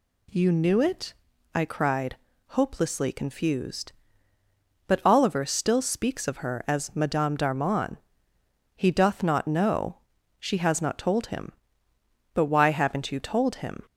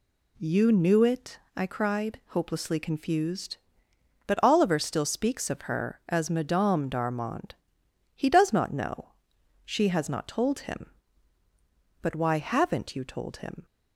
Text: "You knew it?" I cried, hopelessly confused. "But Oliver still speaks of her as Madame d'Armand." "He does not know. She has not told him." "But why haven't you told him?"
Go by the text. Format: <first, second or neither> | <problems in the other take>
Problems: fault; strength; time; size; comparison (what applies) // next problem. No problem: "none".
second | says "doth" for "does"; at 8.9 s